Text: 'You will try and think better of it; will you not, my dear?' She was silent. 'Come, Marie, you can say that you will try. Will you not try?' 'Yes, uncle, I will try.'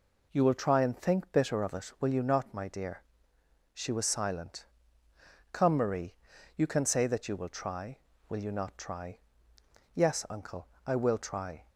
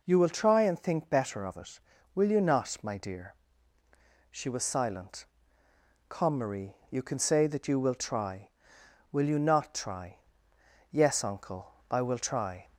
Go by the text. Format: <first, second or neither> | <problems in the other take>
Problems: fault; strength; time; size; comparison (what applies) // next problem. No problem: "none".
second | says "bitter" for "better"; at 1.3 s